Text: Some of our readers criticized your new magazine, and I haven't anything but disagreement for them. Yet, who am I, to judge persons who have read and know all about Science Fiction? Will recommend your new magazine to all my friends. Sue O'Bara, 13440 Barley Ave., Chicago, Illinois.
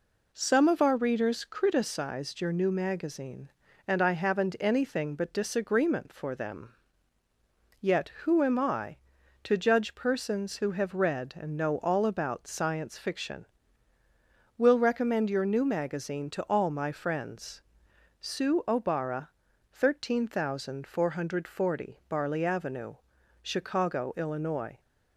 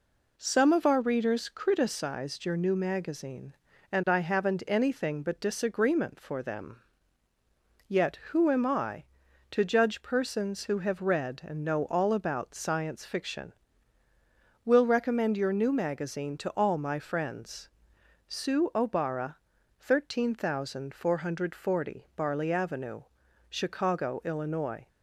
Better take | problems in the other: neither | none

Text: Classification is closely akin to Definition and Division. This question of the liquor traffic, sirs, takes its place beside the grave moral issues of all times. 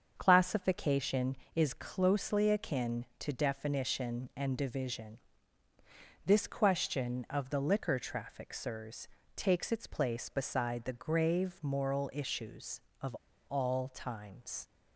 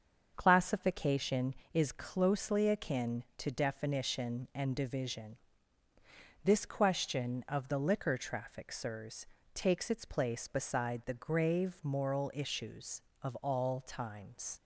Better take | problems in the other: second | starts louder than the rest; until 1.1 s; 7 dB; also in the second // pauses between "of" and "all"; slight; at 13.1 s; 0.31 s long

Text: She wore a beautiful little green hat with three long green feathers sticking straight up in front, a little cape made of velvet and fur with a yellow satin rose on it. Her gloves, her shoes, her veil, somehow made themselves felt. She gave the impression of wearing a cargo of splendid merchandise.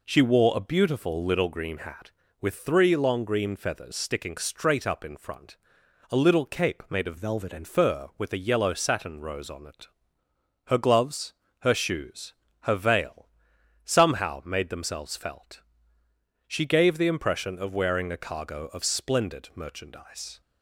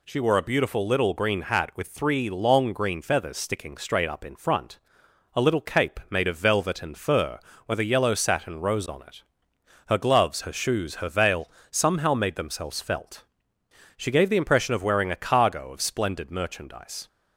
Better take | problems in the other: second | changes voice from "velvet" to "and"; from 7.1 to 7.6 s; 0.5 s long

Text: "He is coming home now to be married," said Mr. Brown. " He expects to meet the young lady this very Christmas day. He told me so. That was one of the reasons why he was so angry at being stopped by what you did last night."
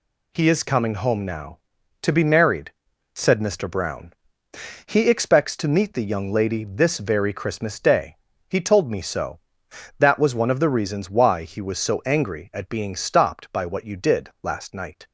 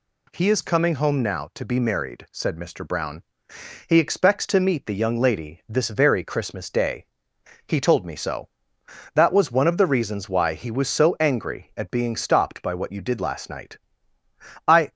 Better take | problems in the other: first | goes on to say "I"; slight; from 14.6 s on; 0.24 s long

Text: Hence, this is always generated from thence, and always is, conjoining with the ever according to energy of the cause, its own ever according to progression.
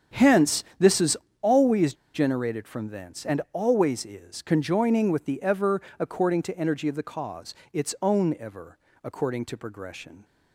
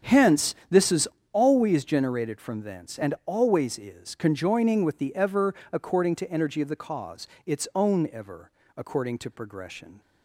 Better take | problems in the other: second | starts louder than the rest; strong; until 1.5 s; 7.5 dB; strong in the second // pauses between "is" and "always"; slight; at 1.1 s; 0.24 s long; slight in the second // pauses between "always" and "generated"; slight; at 1.9 s; 0.19 s long // pauses between "ever" and "according"; slight; at 5.8 s; 0.18 s long; slight in the second // pauses between "ever" and "according"; slight; at 8.7 s; 0.24 s long; slight in the second

